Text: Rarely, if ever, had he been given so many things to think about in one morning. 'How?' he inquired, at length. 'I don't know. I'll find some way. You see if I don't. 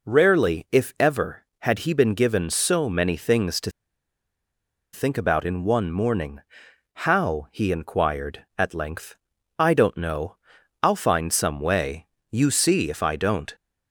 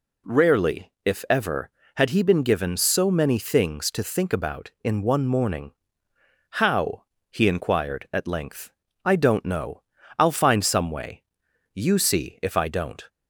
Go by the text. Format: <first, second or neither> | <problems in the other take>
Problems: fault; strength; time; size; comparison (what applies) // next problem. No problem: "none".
second | pauses between "to" and "think"; at 3.7 s; 1.2 s long